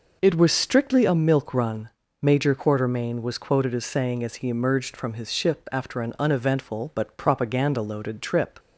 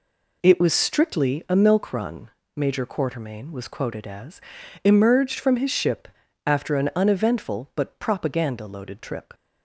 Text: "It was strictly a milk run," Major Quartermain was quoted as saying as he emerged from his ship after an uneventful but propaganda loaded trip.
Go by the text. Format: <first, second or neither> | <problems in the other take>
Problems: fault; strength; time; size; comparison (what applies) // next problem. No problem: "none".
first | skips "saying as he"; at 4.6 s // pauses between "ship" and "after"; at 6.0 s; 0.38 s long